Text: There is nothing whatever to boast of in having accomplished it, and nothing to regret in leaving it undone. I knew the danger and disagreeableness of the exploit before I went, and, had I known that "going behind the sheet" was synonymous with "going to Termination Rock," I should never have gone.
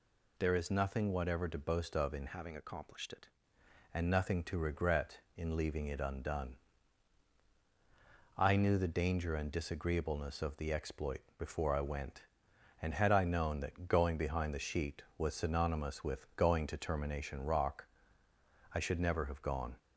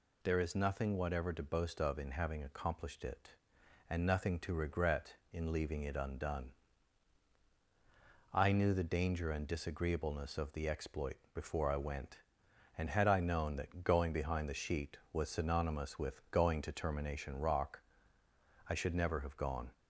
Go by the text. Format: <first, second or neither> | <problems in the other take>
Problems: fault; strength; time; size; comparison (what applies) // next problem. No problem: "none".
second | changes voice from "having" to "it"; from 2.2 to 3.2 s; 1.0 s long // pauses between "exploit" and "before"; slight; at 11.2 s; 0.16 s long; slight in the second